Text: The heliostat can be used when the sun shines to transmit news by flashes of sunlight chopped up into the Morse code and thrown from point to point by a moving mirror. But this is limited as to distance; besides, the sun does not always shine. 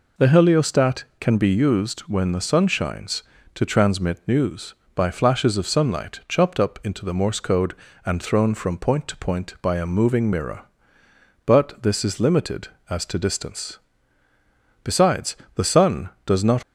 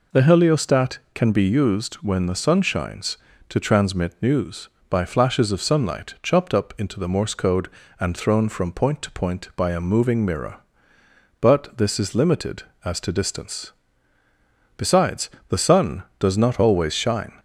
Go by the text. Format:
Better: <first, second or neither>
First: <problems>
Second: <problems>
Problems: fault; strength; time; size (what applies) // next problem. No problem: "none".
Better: second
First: stops before "always shine"; at 16.6 s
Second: none